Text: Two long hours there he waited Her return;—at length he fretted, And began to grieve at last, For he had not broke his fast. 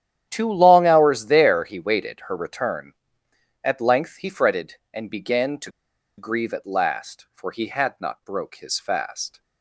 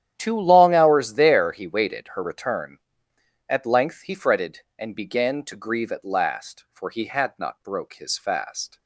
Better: second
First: starts louder than the rest; strong; until 1.3 s; 10.5 dB // pauses between "to" and "grieve"; noticeable; at 5.6 s; 0.48 s long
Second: starts louder than the rest; strong; until 1.1 s; 10.5 dB

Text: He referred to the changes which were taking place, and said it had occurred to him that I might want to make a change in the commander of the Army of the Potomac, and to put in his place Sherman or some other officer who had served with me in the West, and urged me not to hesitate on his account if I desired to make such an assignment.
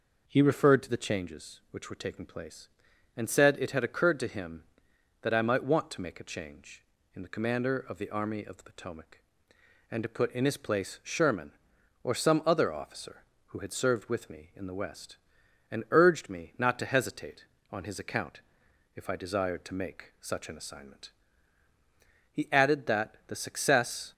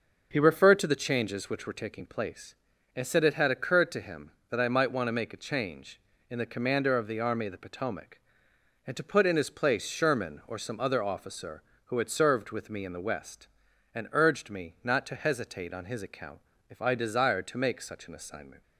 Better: second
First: pauses between "account" and "if"; noticeable; at 18.4 s; 0.54 s long // goes on to say "He added that the success"; strong; from 22.3 s on; 1.8 s long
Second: pauses between "account" and "if"; slight; at 16.3 s; 0.30 s long

